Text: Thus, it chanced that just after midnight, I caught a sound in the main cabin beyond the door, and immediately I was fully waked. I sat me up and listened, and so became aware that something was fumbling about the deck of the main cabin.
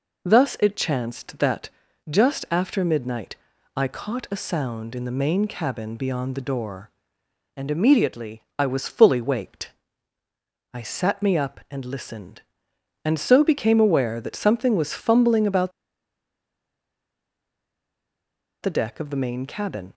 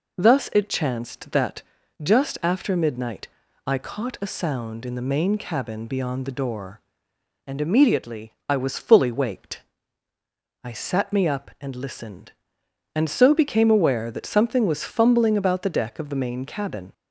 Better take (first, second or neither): second